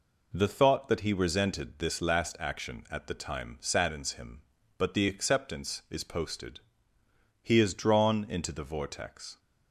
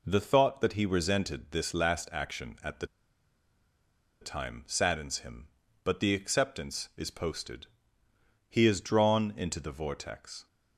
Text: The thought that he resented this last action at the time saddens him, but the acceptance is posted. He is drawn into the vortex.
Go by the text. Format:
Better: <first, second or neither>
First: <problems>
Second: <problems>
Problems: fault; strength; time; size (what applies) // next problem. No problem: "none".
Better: first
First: none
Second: pauses between "the" and "time"; strong; at 2.8 s; 1.3 s long